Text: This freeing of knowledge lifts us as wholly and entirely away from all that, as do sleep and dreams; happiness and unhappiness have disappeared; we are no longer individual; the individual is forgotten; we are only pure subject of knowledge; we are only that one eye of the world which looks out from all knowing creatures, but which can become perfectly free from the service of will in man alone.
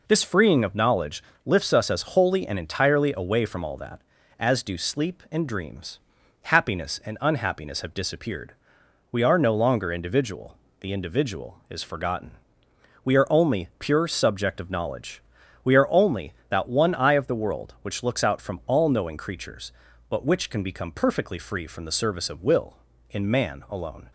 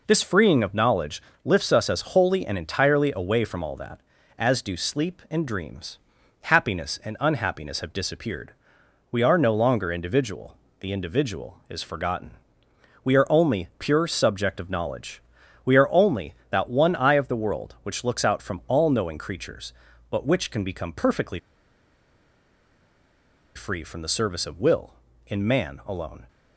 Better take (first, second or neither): first